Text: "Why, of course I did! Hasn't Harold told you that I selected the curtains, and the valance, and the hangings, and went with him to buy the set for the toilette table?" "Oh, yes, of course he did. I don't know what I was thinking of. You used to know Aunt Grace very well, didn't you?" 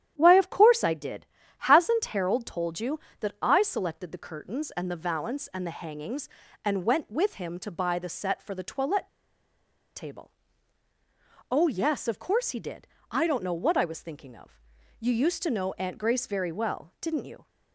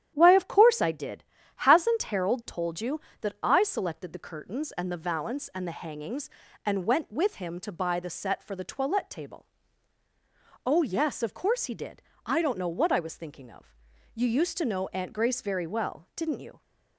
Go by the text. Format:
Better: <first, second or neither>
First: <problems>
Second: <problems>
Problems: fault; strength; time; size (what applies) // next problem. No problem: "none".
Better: second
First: starts louder than the rest; strong; until 1.1 s; 10.5 dB // pauses between "toilette" and "table"; noticeable; at 9.0 s; 0.87 s long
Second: starts louder than the rest; strong; until 1.1 s; 10.5 dB